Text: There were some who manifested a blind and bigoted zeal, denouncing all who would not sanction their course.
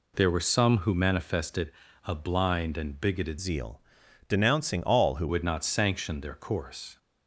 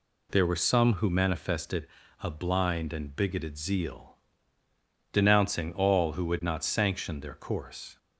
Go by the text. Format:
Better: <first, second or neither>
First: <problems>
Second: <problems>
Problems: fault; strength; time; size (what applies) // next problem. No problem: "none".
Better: second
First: pauses between "manifested" and "a"; slight; at 1.7 s; 0.34 s long // changes voice from "zeal" to "who"; from 3.3 to 5.2 s; 1.9 s long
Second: pauses between "manifested" and "a"; slight; at 1.8 s; 0.34 s long